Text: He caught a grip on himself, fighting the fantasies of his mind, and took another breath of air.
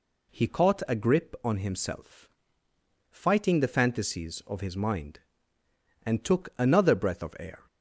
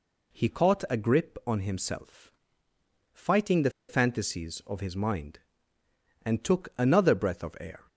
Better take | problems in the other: first | pauses between "the" and "fantasies"; slight; at 3.7 s; 0.18 s long

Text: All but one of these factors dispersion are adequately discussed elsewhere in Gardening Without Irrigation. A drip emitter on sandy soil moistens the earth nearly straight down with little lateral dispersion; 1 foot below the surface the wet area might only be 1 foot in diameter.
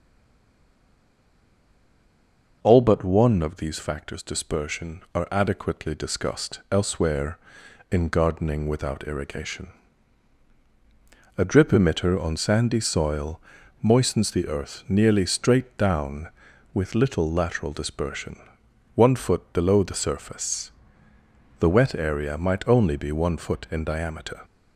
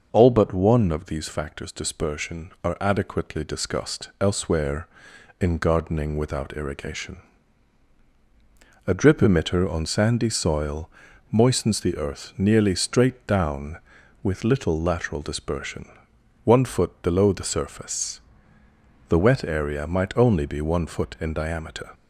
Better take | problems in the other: second | stays silent before the first word; strong; until 2.6 s; 2.6 s long // pauses between "soil" and "moistens"; at 13.4 s; 0.40 s long; also in the second // pauses between "surface" and "the"; noticeable; at 20.7 s; 0.90 s long; noticeable in the second

